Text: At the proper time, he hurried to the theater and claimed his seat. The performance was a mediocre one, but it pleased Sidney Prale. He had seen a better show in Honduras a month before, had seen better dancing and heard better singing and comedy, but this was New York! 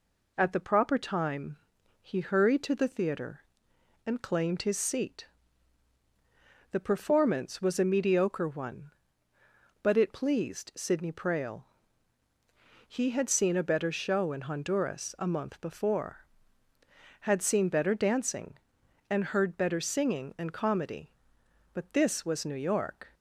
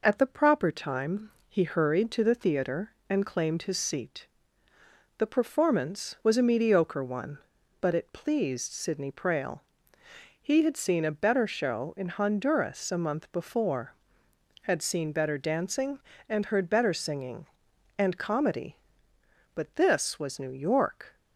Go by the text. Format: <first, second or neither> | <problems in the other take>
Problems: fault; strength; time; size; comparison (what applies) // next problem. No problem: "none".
neither | none